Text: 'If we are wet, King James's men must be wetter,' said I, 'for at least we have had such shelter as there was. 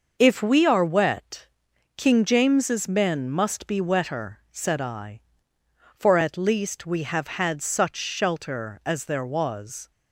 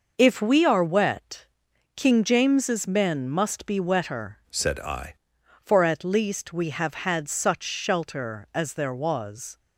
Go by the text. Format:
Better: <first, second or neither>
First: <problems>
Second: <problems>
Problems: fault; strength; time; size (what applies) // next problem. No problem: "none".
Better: first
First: none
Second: changes voice from "said" to "I"; from 4.5 to 5.1 s; 0.6 s long